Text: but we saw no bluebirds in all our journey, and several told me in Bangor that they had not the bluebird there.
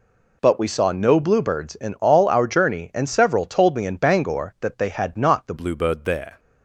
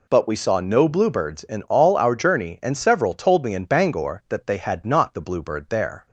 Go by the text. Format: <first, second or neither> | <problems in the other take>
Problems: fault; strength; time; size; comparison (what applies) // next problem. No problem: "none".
second | changes voice at "bluebird"; from 5.5 s on; 0.8 s long